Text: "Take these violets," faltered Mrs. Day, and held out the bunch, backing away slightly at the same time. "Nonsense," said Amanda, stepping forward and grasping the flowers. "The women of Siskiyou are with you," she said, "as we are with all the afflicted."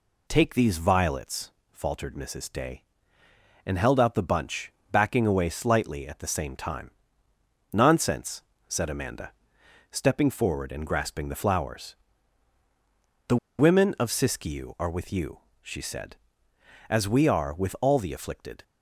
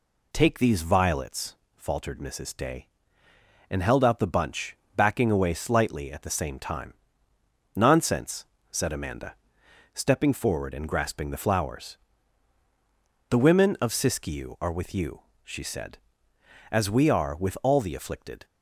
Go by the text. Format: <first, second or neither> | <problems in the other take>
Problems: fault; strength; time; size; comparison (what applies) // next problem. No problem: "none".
second | pauses between "The" and "women"; slight; at 13.3 s; 0.21 s long